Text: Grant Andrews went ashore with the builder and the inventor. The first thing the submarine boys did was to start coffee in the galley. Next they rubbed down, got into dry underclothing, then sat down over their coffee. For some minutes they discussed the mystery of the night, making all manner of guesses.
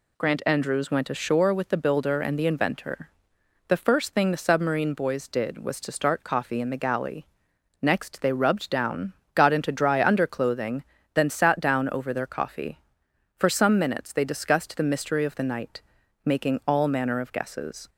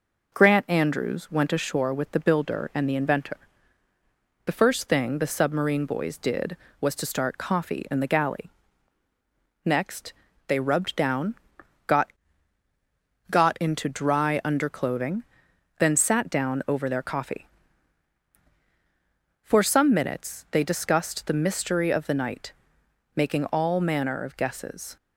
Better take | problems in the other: first | pauses between "Next" and "they"; slight; at 10.1 s; 0.36 s long // says "got" twice; at 13.3 s

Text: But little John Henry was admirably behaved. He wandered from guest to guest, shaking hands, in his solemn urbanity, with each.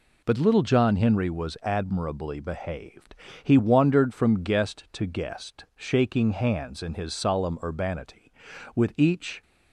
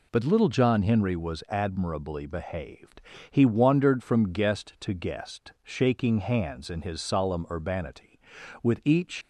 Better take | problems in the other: first | leaves "each" unfinished; at 9.2 s; 75 ms

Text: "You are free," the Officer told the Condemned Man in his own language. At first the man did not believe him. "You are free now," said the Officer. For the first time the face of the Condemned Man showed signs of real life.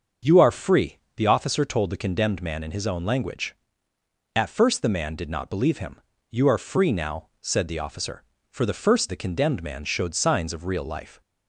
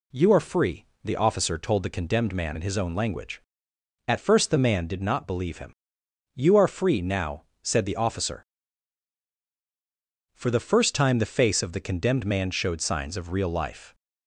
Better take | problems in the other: second | starts louder than the rest; until 1.4 s; 6.5 dB // skips "time the face of"; at 9.0 s

